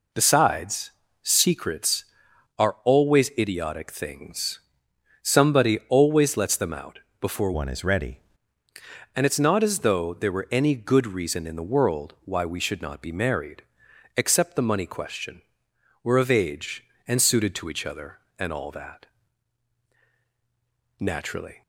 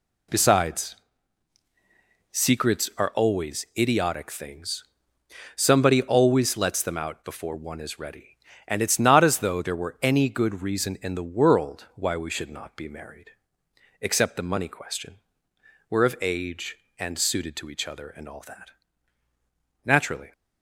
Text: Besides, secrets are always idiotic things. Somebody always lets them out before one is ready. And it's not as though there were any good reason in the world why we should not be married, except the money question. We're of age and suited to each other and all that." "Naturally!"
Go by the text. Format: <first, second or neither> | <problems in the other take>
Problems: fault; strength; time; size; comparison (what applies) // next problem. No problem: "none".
second | pauses between "out" and "before"; slight; at 6.9 s; 0.20 s long // changes voice from "one" to "ready"; from 7.5 to 8.1 s; 0.6 s long